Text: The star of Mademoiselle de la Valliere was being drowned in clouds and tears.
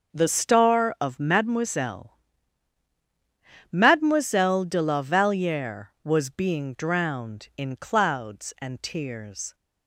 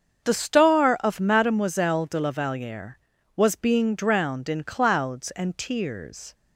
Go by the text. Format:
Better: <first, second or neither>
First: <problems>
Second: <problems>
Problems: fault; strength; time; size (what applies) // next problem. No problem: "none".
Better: second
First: starts louder than the rest; until 1.1 s; 6 dB // says "Mademoiselle" twice; at 3.7 s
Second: starts louder than the rest; until 1.2 s; 7 dB